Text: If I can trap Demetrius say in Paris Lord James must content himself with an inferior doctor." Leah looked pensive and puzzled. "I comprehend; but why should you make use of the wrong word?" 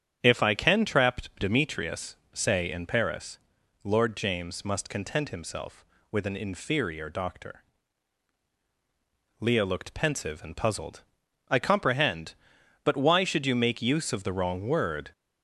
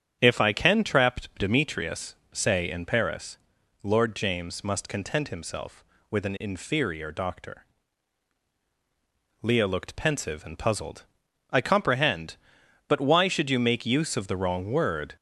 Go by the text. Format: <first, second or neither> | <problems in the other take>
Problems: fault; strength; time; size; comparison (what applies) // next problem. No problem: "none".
neither | starts louder than the rest; strong; the same in both // pauses between "trap" and "Demetrius"; slight; the same in both // pauses between "Demetrius" and "say"; slight; the same in both // pauses between "Paris" and "Lord"; noticeable; the same in both